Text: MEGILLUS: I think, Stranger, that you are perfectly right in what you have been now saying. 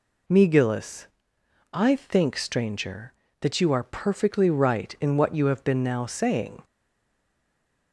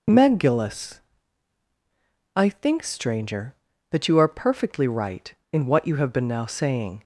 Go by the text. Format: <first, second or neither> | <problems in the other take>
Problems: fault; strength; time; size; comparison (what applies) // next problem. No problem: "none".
second | stays silent after the last word; noticeable; from 6.6 s on; 1.3 s long